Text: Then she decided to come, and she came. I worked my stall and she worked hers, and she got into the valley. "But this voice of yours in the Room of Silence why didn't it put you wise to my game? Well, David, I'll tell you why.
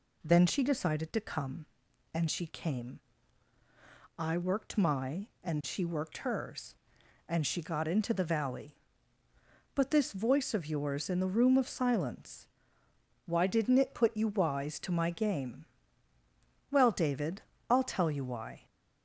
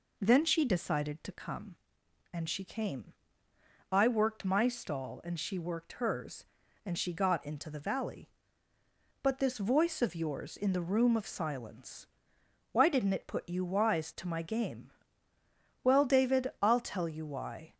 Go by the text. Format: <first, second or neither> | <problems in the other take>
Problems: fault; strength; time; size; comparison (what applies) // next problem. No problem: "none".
second | skips "stall"; at 5.3 s // pauses between "Silence" and "why"; noticeable; at 12.4 s; 0.80 s long; noticeable in the second